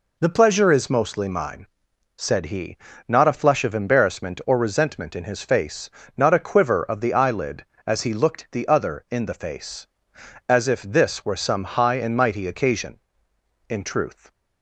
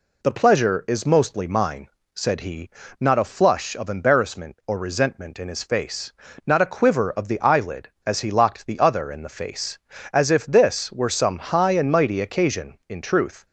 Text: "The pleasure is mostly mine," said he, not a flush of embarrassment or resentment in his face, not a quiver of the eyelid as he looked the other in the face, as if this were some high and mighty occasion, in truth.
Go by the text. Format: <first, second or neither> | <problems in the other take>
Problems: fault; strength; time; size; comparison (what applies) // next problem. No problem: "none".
first | says "locked" for "looked"; at 8.3 s